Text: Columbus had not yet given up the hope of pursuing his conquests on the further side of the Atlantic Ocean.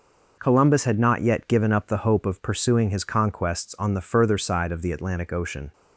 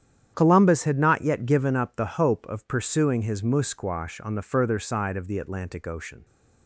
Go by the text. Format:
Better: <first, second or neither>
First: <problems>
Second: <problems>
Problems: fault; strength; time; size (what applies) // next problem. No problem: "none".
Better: first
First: none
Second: starts louder than the rest; strong; until 1.3 s; 9.5 dB // says "musquash" for "conquests"; at 3.4 s